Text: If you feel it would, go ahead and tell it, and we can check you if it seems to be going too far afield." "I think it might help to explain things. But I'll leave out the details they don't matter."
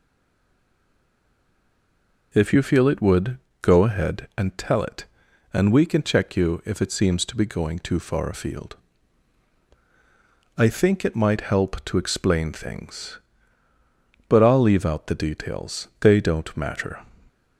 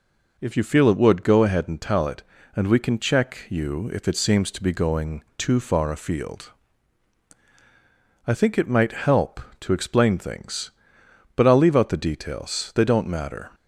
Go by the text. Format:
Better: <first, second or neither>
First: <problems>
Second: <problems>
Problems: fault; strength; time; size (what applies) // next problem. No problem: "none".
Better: second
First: stays silent before the first word; until 2.3 s; 2.3 s long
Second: none